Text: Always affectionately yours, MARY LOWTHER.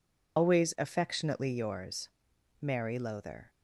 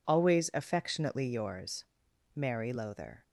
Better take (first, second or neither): second